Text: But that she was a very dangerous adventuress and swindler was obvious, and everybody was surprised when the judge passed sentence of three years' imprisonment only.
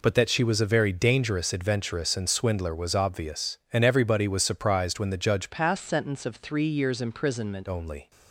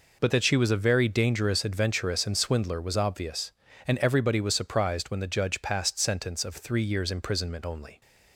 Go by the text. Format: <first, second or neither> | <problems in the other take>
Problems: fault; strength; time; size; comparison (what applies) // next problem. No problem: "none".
second | changes voice from "passed" to "imprisonment"; from 5.5 to 7.6 s; 2.1 s long